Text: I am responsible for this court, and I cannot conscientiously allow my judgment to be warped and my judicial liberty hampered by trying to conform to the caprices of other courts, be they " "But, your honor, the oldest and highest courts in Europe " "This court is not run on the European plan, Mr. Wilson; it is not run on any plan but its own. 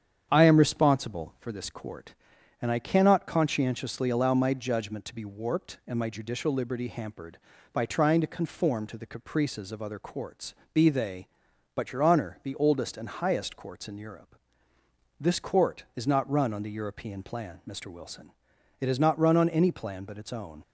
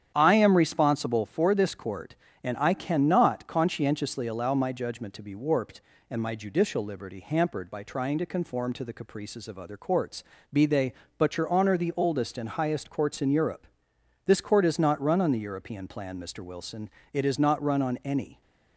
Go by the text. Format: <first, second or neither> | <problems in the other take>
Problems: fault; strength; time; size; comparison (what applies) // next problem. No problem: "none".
first | starts louder than the rest; strong; until 1.1 s; 9 dB; strong in the first // stops before "plan but its own"; at 18.4 s